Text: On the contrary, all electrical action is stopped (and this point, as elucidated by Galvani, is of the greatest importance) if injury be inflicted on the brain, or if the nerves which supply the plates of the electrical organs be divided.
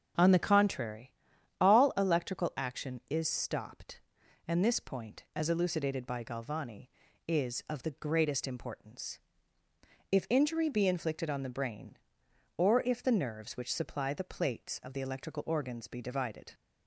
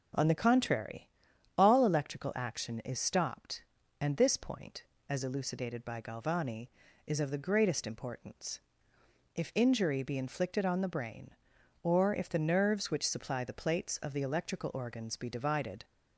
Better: neither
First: starts louder than the rest; strong; until 1.6 s; 7 dB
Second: starts louder than the rest; until 1.6 s; 6.5 dB

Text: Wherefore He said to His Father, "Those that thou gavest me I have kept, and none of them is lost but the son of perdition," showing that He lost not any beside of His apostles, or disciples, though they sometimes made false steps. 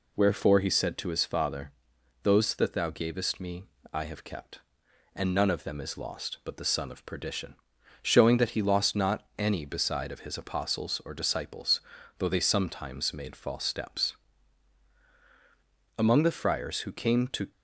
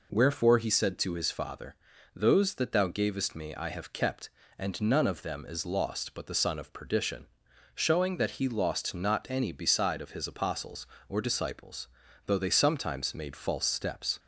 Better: second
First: pauses between "me" and "I"; slight; at 3.6 s; 0.26 s long // goes on to say "Among the friars who came to"; from 15.9 s on; 1.5 s long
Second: none

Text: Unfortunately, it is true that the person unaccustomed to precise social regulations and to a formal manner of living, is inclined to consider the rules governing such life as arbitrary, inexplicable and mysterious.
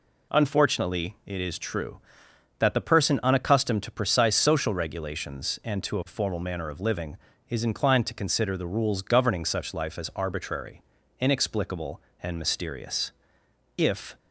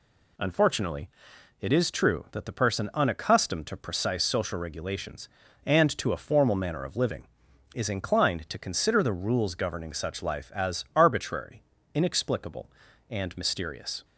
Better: second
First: goes on to say "If"; slight; from 13.7 s on; 0.40 s long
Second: none

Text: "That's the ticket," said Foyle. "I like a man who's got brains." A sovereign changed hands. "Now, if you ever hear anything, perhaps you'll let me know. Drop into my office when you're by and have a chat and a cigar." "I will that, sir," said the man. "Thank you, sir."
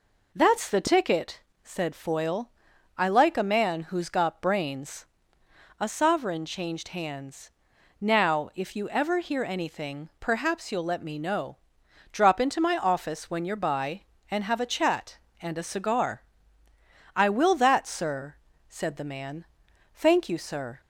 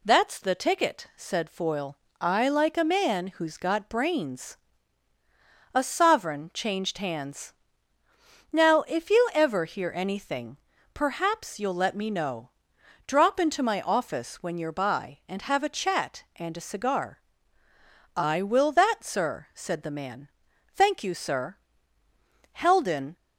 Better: first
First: none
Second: goes on to say "Heldon"; noticeable; from 22.5 s on; 0.64 s long

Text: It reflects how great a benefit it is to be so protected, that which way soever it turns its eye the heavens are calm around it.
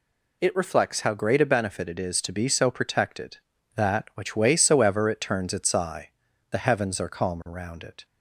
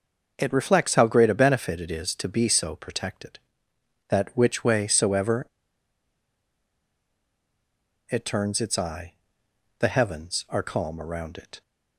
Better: first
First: pauses between "eye" and "the"; at 6.0 s; 0.42 s long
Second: pauses between "soever" and "it"; strong; at 5.4 s; 2.6 s long // pauses between "eye" and "the"; noticeable; at 9.1 s; 0.66 s long

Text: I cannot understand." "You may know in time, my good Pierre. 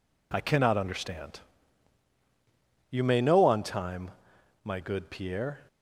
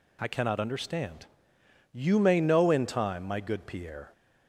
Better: second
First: says "on" for "in"; at 3.4 s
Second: none

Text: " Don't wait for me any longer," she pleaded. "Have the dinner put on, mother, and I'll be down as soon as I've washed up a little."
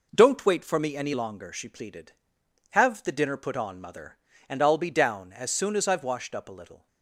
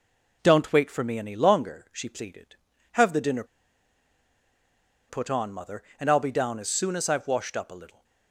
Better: first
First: none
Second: pauses between "dinner" and "put"; strong; at 3.4 s; 1.6 s long

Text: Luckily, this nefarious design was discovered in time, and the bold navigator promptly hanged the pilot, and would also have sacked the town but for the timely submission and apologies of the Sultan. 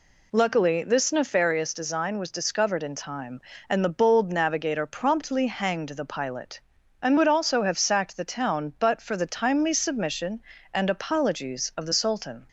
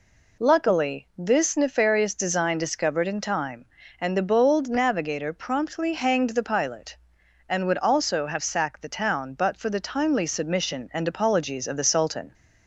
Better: first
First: none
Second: skips "was"; at 2.5 s

